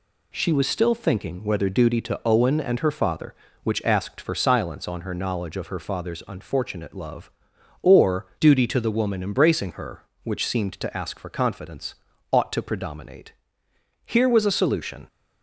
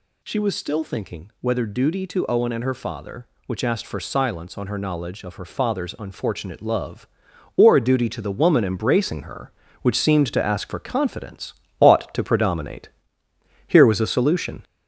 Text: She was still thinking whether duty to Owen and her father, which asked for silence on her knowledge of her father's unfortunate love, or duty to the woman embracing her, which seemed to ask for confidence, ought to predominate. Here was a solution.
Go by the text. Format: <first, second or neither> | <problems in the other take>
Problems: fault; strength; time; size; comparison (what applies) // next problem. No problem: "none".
first | gets louder; noticeable; throughout; 5 dB